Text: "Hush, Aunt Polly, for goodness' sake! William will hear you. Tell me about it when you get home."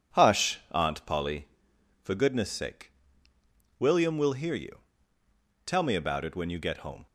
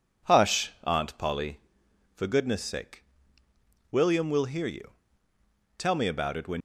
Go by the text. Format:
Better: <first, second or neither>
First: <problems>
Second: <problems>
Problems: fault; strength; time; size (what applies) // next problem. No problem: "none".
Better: first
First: none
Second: stops before "you get home"; at 6.5 s